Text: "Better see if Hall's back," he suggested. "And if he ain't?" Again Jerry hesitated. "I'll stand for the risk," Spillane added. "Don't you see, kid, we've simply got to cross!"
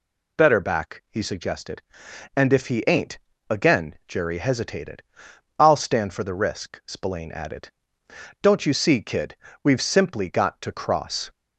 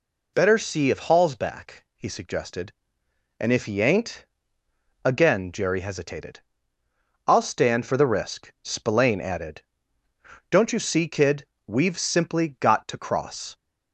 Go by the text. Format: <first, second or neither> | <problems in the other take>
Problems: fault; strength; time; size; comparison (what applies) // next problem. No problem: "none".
second | skips "see if Hall's"; at 0.5 s